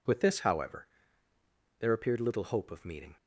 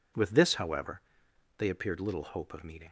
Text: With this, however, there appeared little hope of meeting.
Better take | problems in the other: first | says "they" for "there"; at 1.5 s

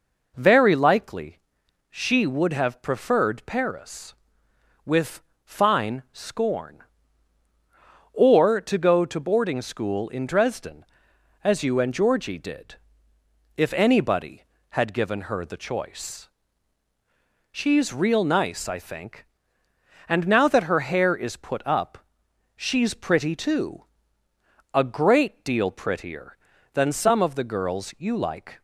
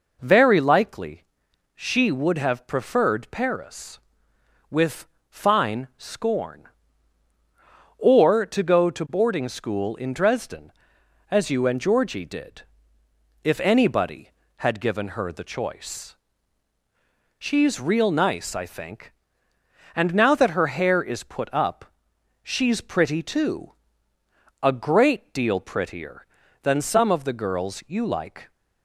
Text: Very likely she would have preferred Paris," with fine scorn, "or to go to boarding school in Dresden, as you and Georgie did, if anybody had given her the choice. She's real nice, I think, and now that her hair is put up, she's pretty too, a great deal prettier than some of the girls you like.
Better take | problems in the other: neither | pauses between "likely" and "she"; noticeable; the same in both // pauses between "with" and "fine"; slight; the same in both

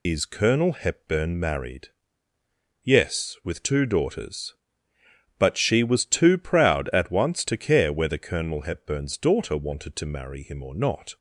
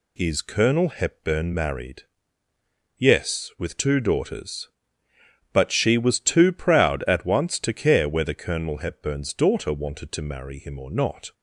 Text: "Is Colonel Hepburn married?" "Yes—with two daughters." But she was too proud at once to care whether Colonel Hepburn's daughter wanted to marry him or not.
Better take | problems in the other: second | loses the start of "Is"; at 0.0 s; 45 ms

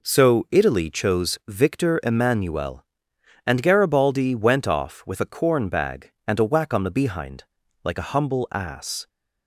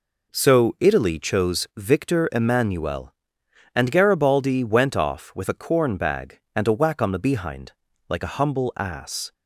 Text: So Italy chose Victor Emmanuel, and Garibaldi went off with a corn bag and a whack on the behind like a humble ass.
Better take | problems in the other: neither | pauses between "behind" and "like"; the same in both

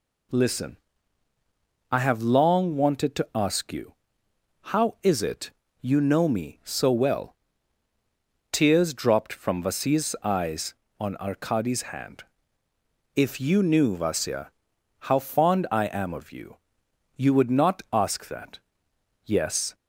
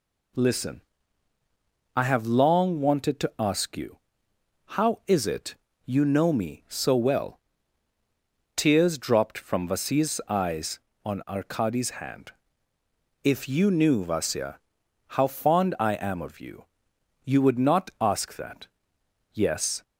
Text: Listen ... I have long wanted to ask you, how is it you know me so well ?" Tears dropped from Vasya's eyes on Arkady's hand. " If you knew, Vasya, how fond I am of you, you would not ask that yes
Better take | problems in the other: neither | pauses between "it" and "you"; slight; the same in both // pauses between "that" and "yes"; noticeable; the same in both

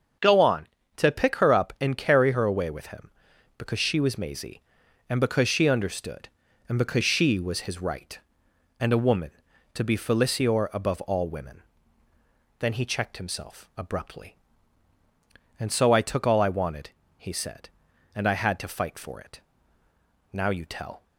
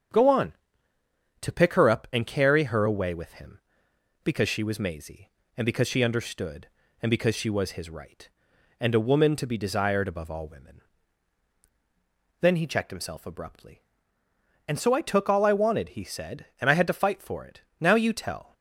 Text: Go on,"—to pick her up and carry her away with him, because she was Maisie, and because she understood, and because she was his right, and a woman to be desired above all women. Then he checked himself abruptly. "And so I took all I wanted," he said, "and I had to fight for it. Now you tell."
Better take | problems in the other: second | starts louder than the rest; until 1.5 s; 7 dB; strong in the second // says "felicior" for "desired"; at 9.9 s

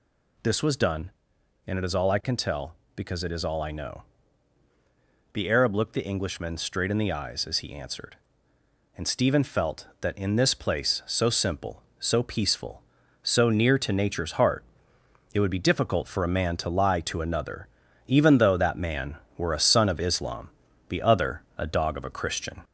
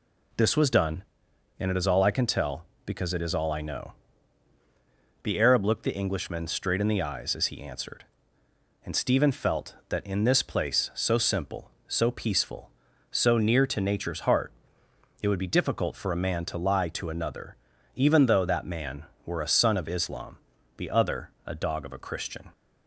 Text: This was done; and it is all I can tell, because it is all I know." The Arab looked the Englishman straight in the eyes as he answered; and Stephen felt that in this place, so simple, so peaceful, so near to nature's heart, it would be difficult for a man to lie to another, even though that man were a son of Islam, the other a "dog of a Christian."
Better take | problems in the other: second | gets louder; slight; throughout; 2.5 dB // pauses between "other" and "a"; slight; at 21.4 s; 0.16 s long; slight in the second

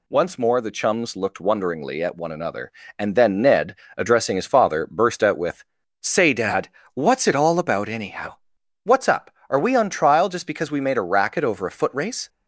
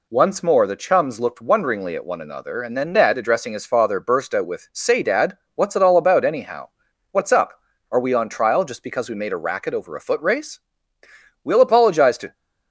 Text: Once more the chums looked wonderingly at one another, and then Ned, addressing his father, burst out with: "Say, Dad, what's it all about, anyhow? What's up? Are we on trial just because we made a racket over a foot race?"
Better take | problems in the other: first | goes on to say "We'll apologize to"; noticeable; from 11.4 s on; 0.90 s long

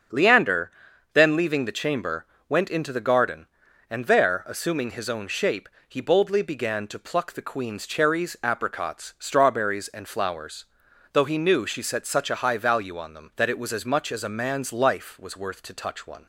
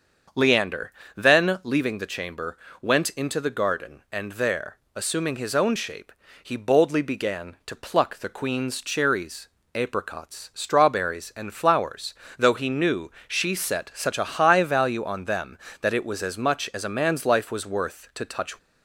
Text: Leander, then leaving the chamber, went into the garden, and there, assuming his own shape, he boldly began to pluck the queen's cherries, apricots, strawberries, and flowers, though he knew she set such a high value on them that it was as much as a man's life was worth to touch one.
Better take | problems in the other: first | starts louder than the rest; until 1.5 s; 7 dB; also in the first // pauses between "knew" and "she"; slight; at 13.0 s; 0.18 s long // stops before "one"; at 18.5 s

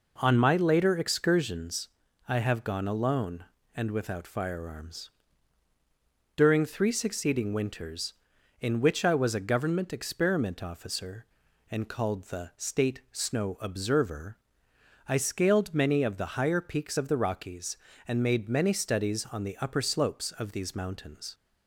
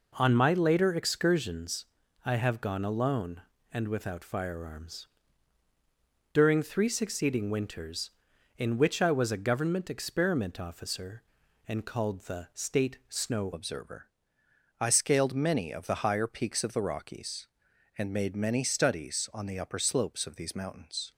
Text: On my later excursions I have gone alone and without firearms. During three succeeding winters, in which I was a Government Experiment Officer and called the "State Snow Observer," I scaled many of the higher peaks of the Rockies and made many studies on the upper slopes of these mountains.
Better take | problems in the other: first | pauses between "excursions" and "I"; at 1.8 s; 0.38 s long; also in the first // changes voice at "Observer"; from 13.5 s on; 7.6 s long

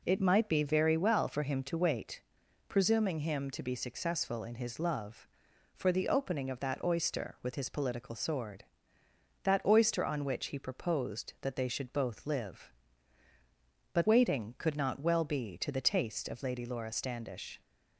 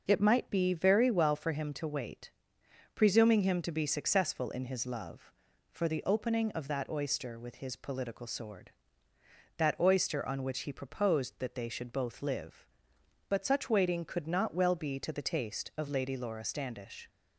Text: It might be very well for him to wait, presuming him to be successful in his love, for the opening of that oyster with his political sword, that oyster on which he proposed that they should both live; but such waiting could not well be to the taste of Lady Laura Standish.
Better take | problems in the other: second | skips "such"; at 14.0 s

